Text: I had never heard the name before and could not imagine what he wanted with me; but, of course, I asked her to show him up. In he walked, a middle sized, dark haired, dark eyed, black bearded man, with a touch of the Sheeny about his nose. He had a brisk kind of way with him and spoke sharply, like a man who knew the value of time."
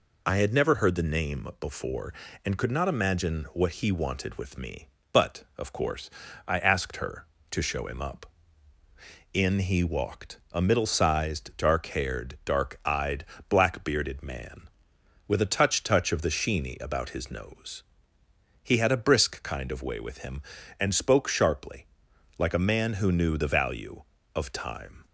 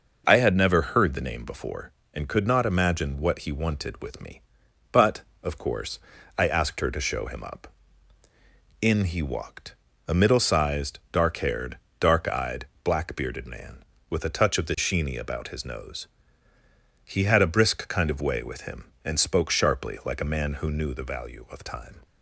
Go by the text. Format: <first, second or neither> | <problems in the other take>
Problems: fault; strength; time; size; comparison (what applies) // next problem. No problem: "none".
second | says "touch" twice; at 15.8 s